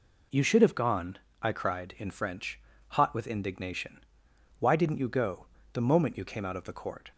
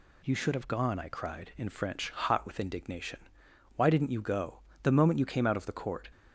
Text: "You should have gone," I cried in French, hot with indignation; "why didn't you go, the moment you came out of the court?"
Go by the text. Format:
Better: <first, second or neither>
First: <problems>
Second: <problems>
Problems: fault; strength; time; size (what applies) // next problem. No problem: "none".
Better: neither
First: none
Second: none